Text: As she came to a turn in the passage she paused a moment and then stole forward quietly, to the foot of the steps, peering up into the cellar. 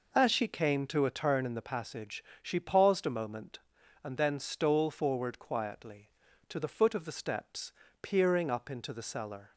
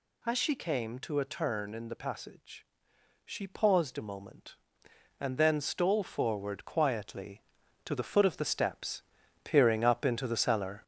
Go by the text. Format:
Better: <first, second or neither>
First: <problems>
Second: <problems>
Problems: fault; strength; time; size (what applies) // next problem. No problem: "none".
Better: first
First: pauses between "passage" and "she"; slight; at 2.2 s; 0.20 s long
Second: gets louder; noticeable; throughout; 5.5 dB // pauses between "passage" and "she"; noticeable; at 2.6 s; 0.60 s long